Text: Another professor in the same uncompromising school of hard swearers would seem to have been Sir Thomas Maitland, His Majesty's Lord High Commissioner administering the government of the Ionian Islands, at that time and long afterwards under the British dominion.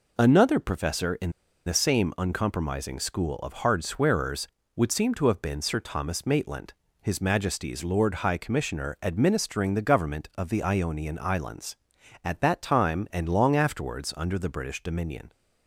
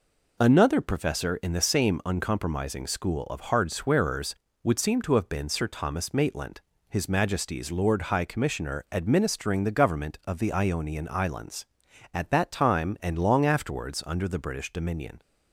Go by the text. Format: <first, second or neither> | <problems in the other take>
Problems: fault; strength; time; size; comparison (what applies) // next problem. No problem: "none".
second | pauses between "in" and "the"; slight; at 1.3 s; 0.35 s long